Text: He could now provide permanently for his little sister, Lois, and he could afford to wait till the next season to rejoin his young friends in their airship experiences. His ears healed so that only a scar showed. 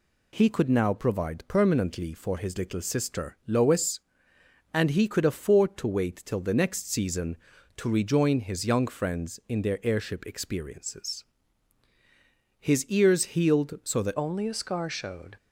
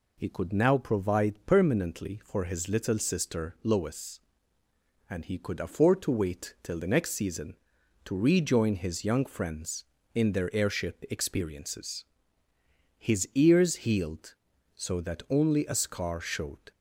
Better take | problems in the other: second | changes voice at "only"; from 14.1 s on; 1.2 s long

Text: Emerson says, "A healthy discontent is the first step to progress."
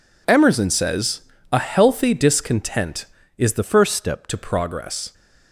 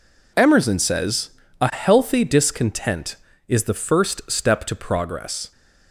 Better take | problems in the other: second | changes voice from "first" to "step"; from 3.6 to 4.2 s; 0.6 s long

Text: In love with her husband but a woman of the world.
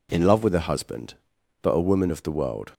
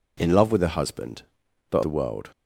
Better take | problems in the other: first | skips "a woman of"; at 1.8 s

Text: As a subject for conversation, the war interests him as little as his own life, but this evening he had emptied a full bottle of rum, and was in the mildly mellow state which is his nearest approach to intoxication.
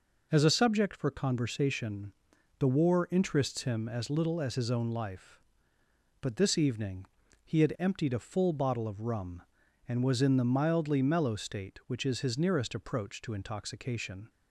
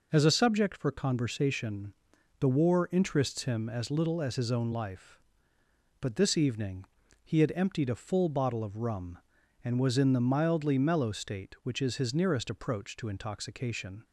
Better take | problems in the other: neither | pauses between "evening" and "he"; the same in both

